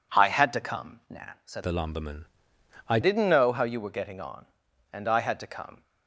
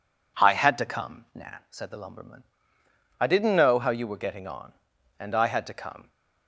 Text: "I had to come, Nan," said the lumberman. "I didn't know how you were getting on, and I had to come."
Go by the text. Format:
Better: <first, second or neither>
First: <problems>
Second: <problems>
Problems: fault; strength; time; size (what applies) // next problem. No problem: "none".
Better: second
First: changes voice from "the" to "I"; from 1.6 to 2.9 s; 1.3 s long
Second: none